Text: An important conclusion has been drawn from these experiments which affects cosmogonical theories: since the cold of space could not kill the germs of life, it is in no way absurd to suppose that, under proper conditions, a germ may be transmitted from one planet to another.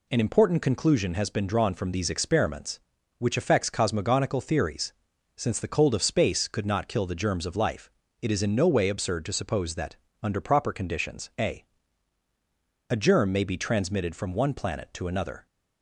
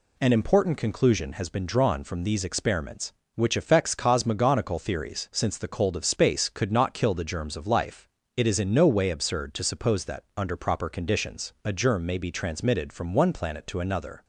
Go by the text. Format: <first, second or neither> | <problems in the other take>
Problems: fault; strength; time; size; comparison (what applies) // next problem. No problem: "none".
second | says "a" twice; at 12.8 s